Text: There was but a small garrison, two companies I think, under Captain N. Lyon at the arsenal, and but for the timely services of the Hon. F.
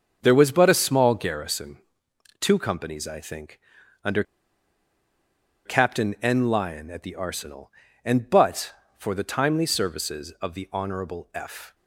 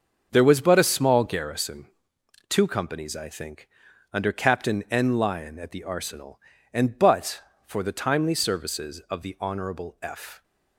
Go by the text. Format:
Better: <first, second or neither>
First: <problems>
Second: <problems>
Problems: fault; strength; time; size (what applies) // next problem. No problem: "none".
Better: second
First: starts louder than the rest; until 1.2 s; 6.5 dB // pauses between "under" and "Captain"; strong; at 4.2 s; 1.4 s long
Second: starts louder than the rest; until 1.3 s; 6.5 dB